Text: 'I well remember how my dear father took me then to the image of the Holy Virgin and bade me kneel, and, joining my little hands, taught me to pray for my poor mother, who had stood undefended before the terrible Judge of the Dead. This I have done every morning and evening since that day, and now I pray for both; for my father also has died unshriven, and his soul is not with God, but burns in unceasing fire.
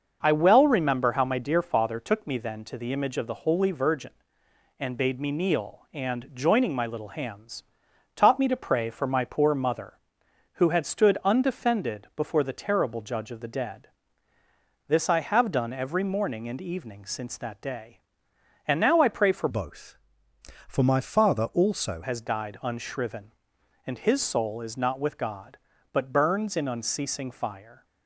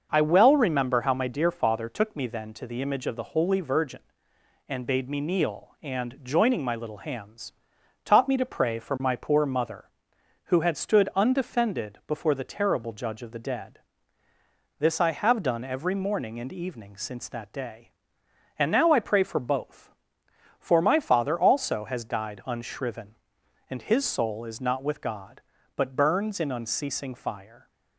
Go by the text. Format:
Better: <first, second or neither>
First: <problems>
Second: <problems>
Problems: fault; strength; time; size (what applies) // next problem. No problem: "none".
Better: second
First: starts louder than the rest; noticeable; until 1.2 s; 6 dB // changes voice from "both" to "also"; from 19.4 to 22.0 s; 2.6 s long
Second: starts louder than the rest; noticeable; until 1.1 s; 6 dB